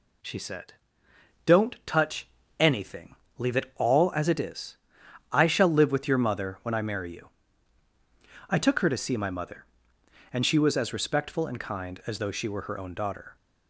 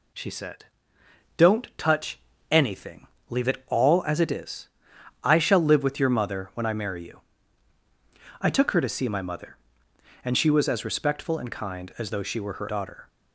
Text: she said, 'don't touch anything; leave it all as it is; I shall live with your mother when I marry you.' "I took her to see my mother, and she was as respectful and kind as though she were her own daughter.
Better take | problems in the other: first | pauses between "touch" and "anything"; slight; at 2.1 s; 0.30 s long; slight in the first // skips "own"; at 12.6 s

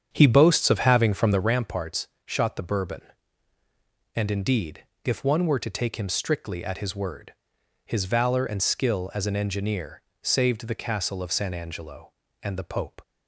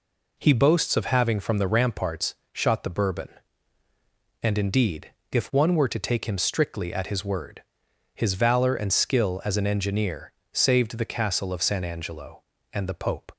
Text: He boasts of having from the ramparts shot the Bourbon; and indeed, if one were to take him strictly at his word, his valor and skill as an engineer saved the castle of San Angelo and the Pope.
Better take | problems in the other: second | starts louder than the rest; strong; until 1.5 s; 8 dB // pauses between "ramparts" and "shot"; slight; at 2.0 s; 0.18 s long; slight in the second // pauses between "engineer" and "saved"; slight; at 10.0 s; 0.20 s long; slight in the second

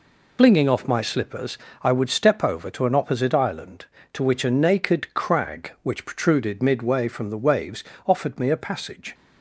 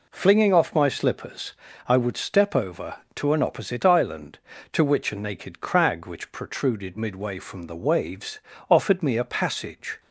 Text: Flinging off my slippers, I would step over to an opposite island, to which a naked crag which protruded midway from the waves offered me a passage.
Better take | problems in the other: second | loses the start of "Flinging"; at 0.3 s; 60 ms // pauses between "waves" and "offered"; slight; at 7.8 s; 0.24 s long; slight in the second

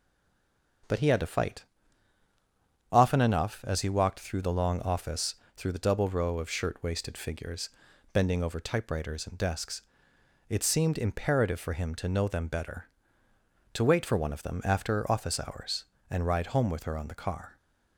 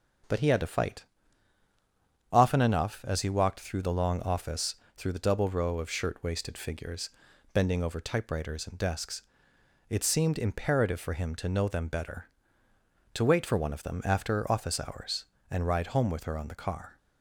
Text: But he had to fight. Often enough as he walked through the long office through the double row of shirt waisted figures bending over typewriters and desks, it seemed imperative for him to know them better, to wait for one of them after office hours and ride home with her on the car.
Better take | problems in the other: second | stays silent before the first word; slight; until 0.8 s; 0.8 s long // starts louder than the rest; until 3.1 s; 7 dB; also in the second // pauses between "office" and "through"; slight; at 5.3 s; 0.22 s long; slight in the second // pauses between "figures" and "bending"; at 7.6 s; 0.44 s long; also in the second

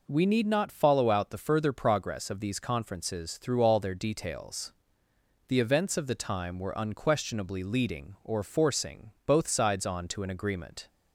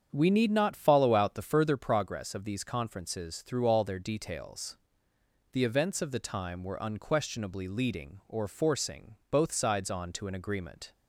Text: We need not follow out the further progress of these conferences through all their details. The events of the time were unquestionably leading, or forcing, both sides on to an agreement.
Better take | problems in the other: first | starts louder than the rest; strong; until 1.8 s; 7.5 dB

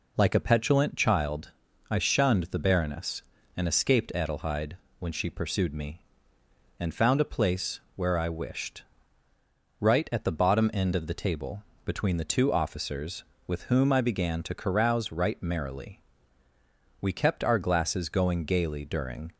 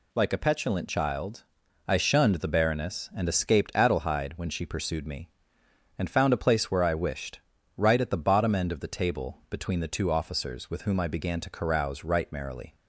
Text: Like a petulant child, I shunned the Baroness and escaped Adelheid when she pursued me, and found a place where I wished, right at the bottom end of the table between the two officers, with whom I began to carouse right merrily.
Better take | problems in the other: second | pauses between "Adelheid" and "when"; slight; at 4.7 s; 0.20 s long // pauses between "place" and "where"; slight; at 7.8 s; 0.16 s long // pauses between "table" and "between"; slight; at 11.6 s; 0.20 s long // goes on to say "We kept our glasses going gaily during"; strong; from 17.0 s on; 2.3 s long

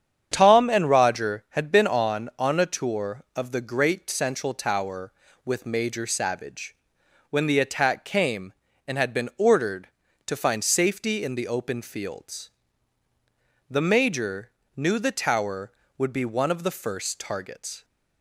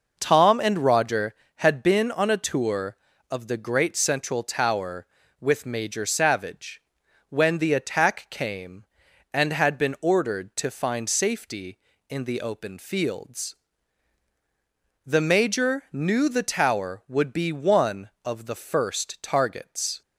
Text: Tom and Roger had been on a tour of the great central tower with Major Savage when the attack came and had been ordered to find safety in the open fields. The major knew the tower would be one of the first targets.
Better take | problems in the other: second | starts louder than the rest; strong; until 1.3 s; 8.5 dB // says "on" twice; at 2.3 s // pauses between "Savage" and "when"; noticeable; at 6.7 s; 0.54 s long; noticeable in the second // pauses between "major" and "knew"; slight; at 14.4 s; 0.26 s long

